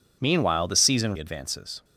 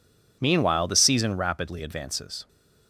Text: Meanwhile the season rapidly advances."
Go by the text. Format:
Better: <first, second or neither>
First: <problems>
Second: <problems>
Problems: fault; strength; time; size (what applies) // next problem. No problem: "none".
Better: second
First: skips "rapidly"; at 1.1 s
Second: none